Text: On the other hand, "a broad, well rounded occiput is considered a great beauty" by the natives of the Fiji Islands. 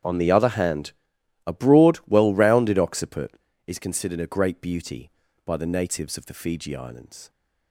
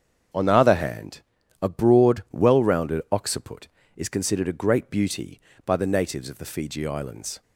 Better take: neither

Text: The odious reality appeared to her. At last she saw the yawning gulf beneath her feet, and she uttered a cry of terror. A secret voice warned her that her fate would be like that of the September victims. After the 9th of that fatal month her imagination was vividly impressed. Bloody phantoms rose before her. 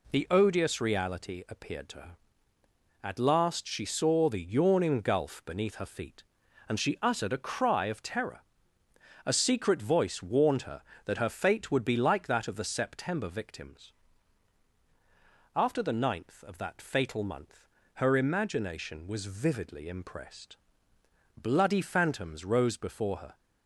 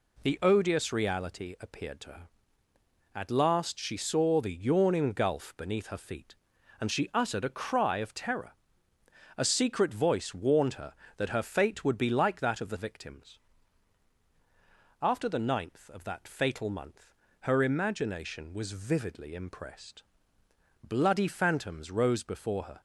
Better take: first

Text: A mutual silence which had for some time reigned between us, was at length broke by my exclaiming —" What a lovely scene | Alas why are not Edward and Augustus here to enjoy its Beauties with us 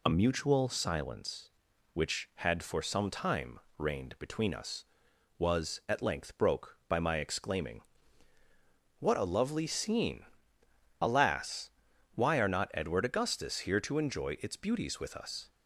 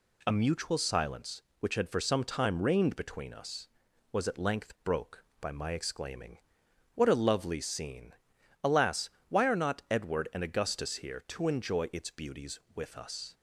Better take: second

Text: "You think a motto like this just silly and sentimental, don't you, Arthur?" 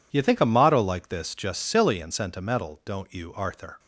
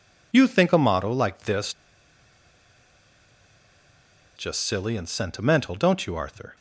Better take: first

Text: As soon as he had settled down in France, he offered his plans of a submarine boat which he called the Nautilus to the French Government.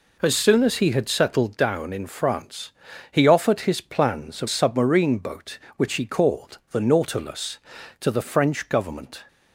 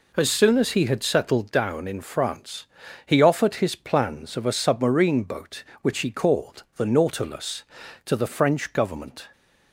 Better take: second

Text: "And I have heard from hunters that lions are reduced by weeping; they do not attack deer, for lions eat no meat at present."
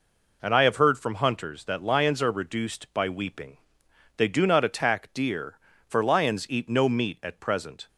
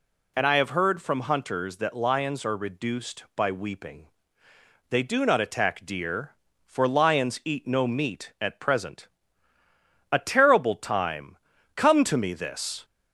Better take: first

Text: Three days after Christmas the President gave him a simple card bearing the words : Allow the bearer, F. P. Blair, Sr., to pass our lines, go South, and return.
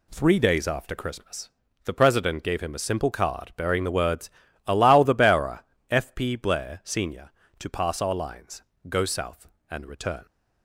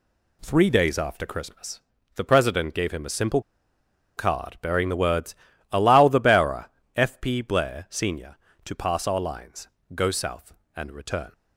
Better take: first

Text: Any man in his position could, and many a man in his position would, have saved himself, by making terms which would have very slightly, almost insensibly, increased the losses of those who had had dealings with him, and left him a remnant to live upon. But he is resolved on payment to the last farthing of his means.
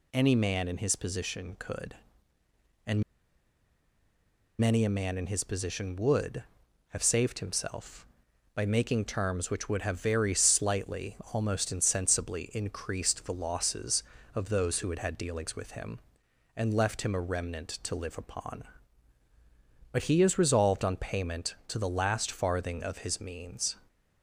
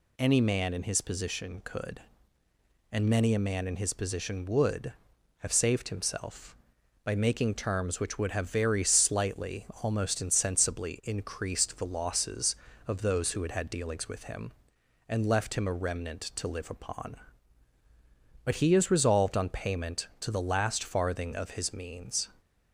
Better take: second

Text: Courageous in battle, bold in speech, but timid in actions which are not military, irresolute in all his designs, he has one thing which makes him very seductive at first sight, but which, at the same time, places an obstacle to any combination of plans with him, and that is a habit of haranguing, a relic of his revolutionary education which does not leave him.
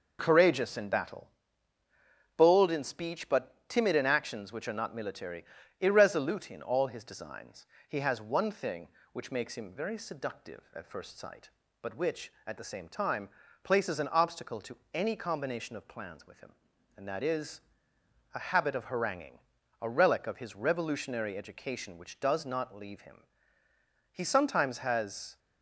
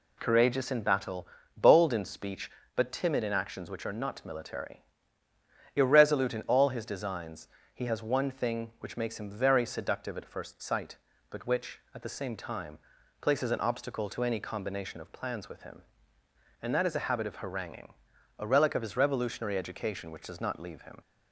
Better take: second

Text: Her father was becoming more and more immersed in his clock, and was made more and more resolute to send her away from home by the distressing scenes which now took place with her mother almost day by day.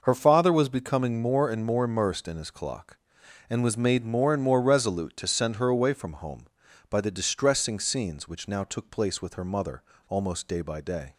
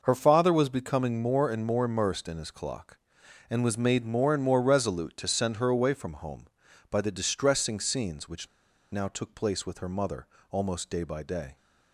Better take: first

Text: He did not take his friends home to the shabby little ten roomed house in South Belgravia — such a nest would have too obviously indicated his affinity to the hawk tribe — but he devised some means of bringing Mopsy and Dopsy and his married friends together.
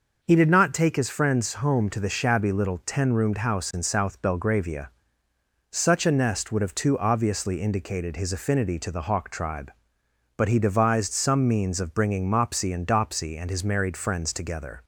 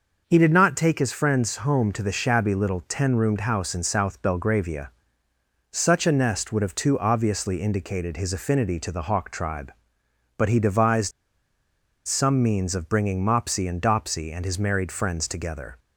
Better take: first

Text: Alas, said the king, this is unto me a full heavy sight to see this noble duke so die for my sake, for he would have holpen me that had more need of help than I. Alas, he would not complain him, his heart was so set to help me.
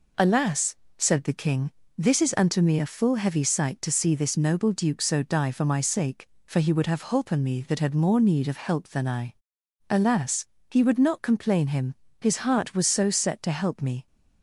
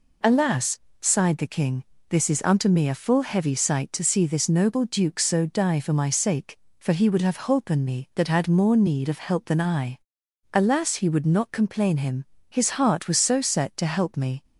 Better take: first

